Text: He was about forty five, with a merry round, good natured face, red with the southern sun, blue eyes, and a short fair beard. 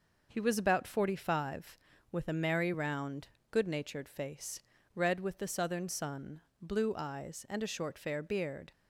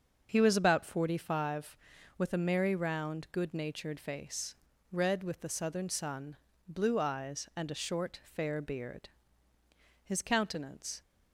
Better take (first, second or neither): first